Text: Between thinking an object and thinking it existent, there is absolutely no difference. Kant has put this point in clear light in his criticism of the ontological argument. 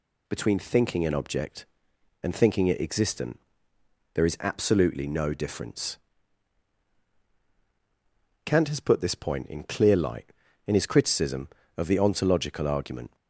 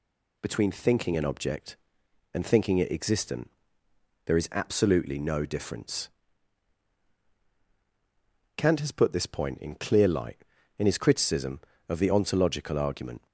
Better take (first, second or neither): neither